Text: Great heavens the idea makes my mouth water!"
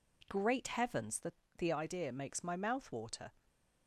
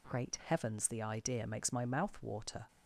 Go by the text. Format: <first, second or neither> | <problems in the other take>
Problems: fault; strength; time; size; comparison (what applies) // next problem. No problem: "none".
second | says "the" twice; at 1.5 s